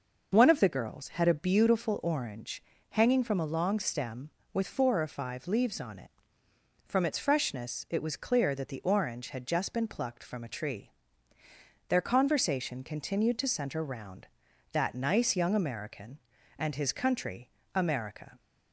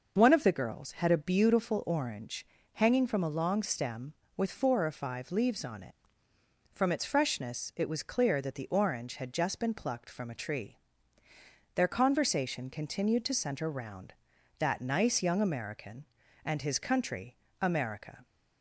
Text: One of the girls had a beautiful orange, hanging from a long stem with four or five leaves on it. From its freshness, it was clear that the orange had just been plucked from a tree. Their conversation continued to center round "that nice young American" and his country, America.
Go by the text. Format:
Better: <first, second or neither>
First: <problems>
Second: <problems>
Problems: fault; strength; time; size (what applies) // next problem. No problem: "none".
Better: neither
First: none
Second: none